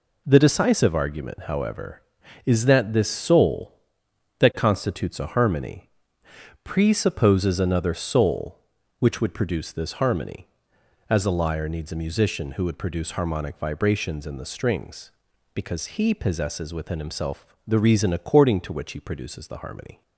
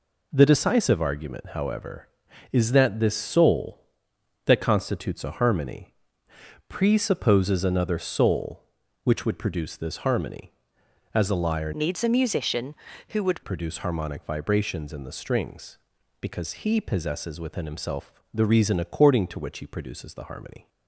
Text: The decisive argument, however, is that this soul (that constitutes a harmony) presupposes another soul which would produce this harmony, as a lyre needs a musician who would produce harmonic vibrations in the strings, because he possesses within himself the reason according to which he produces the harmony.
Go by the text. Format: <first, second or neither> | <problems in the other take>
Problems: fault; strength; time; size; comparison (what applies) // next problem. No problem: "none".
first | changes voice from "needs" to "would"; from 11.7 to 13.4 s; 1.7 s long